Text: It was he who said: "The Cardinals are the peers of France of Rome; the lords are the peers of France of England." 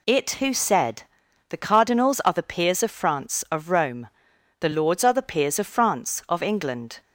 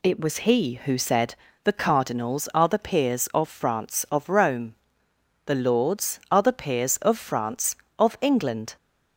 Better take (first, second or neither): second